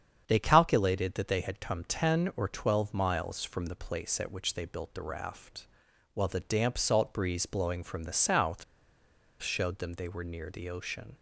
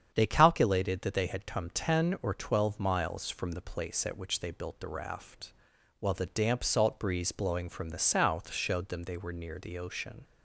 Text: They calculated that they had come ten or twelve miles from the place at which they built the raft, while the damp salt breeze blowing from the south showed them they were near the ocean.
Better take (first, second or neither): second